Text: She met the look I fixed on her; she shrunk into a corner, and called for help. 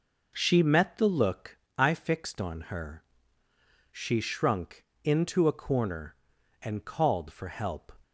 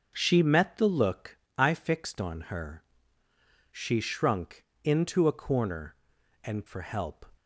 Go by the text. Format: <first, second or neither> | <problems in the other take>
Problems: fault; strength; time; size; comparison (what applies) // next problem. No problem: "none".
first | pauses between "look" and "I"; slight; at 1.3 s; 0.22 s long; slight in the first // pauses between "shrunk" and "into"; slight; at 4.6 s; 0.20 s long; slight in the first // skips "called"; at 6.6 s